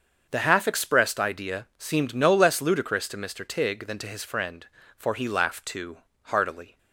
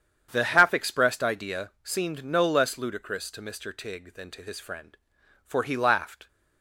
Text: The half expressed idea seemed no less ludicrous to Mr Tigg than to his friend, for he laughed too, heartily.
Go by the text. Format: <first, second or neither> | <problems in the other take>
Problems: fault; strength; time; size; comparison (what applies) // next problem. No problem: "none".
first | starts louder than the rest; strong; until 1.3 s; 8.5 dB; also in the first // stops before "too heartily"; at 6.2 s